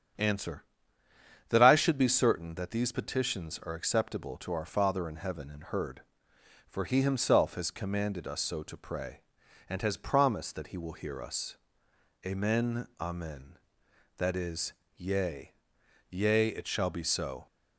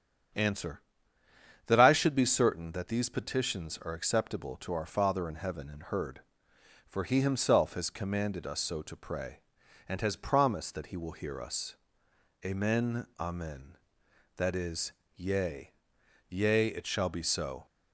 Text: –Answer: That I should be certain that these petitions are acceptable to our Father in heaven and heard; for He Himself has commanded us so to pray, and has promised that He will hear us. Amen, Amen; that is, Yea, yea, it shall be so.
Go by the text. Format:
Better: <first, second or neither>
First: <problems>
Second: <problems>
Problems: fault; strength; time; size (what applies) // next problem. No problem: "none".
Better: neither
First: starts louder than the rest; strong; until 2.0 s; 8 dB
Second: starts louder than the rest; strong; until 2.2 s; 8 dB